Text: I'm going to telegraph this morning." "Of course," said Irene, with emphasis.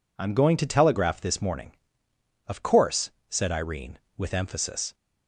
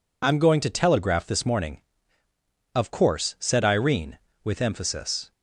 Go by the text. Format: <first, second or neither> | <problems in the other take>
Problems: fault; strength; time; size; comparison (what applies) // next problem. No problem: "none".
neither | none